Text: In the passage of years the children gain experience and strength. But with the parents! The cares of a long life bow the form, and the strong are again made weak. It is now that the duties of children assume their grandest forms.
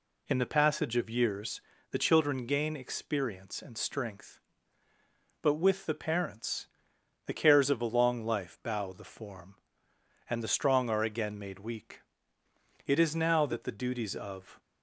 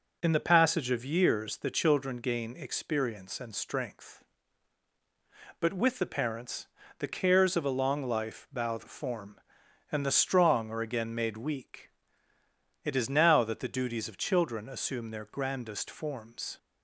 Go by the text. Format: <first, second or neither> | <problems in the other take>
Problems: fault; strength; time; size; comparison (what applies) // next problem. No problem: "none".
second | pauses between "years" and "the"; slight; at 1.6 s; 0.30 s long // stops before "children assume their grandest forms"; at 14.5 s